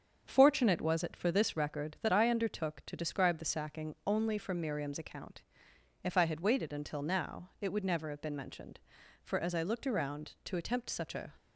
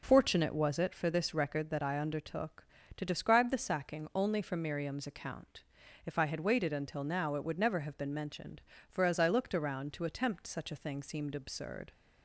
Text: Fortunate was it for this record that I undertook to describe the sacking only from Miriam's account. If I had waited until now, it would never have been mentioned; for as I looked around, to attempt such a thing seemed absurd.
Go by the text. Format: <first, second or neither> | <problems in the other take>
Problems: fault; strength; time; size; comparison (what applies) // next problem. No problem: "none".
second | starts louder than the rest; until 1.2 s; 7 dB // stops before "thing seemed absurd"; at 11.3 s